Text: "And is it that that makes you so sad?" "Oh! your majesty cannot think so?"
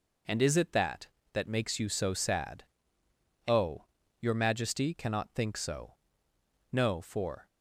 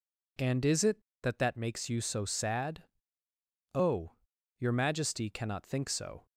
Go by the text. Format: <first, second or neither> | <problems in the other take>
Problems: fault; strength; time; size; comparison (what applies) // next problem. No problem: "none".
second | goes on to say "No for"; noticeable; from 6.7 s on; 0.74 s long